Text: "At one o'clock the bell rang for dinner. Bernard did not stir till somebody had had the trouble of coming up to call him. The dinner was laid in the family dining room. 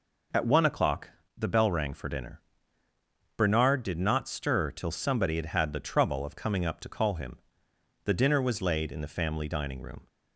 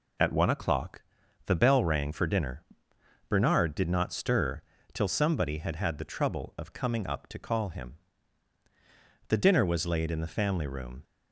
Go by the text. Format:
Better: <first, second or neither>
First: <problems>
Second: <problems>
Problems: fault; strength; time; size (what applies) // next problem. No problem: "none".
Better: first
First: pauses between "o'clock" and "the"; slight; at 1.0 s; 0.26 s long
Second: pauses between "o'clock" and "the"; at 1.0 s; 0.44 s long // pauses between "stir" and "till"; slight; at 4.6 s; 0.32 s long // skips "dining"; at 10.6 s